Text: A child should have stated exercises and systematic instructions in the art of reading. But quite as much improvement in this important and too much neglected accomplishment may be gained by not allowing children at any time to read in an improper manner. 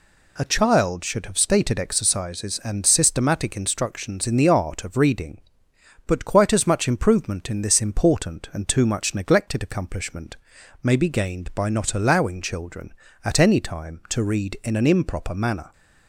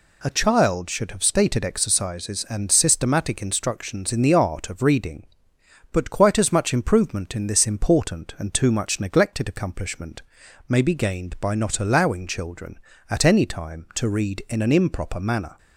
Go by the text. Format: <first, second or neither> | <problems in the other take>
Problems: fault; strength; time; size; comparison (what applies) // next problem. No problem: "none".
neither | pauses between "accomplishment" and "may"; noticeable; the same in both